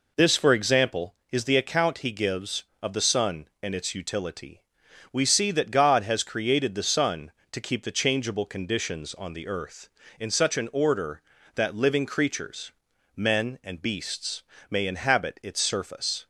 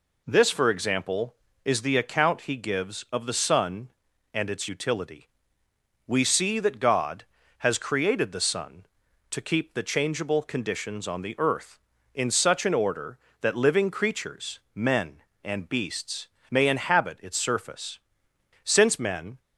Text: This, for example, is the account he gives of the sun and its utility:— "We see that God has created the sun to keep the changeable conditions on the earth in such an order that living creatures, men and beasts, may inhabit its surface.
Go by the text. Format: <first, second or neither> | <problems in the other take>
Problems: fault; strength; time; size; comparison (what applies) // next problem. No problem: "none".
first | goes on to say "Since men"; noticeable; from 18.6 s on; 0.76 s long